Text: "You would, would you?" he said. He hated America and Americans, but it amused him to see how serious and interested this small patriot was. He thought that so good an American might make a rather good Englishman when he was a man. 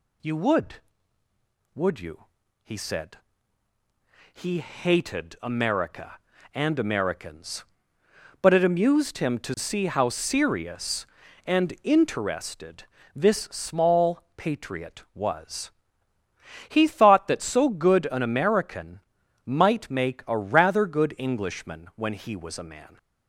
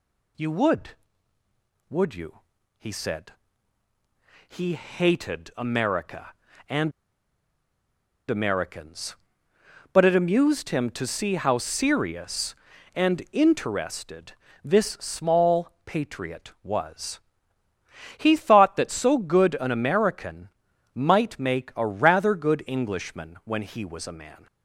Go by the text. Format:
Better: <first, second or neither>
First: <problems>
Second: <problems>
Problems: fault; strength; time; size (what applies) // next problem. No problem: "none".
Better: first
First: pauses between "interested" and "this"; slight; at 12.8 s; 0.30 s long // pauses between "small" and "patriot"; slight; at 14.2 s; 0.16 s long // pauses between "American" and "might"; noticeable; at 18.9 s; 0.46 s long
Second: pauses between "and" and "Americans"; strong; at 6.9 s; 1.3 s long // pauses between "interested" and "this"; slight; at 14.3 s; 0.30 s long // pauses between "small" and "patriot"; slight; at 15.7 s; 0.16 s long // pauses between "American" and "might"; noticeable; at 20.4 s; 0.46 s long